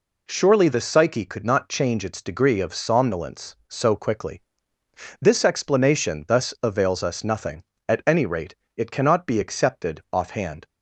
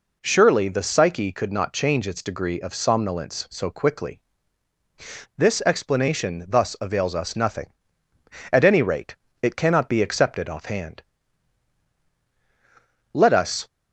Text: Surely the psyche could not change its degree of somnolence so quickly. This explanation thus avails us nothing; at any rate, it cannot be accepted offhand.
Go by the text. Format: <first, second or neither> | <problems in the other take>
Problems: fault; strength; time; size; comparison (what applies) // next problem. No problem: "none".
first | goes on to say "Let us"; from 13.1 s on; 0.54 s long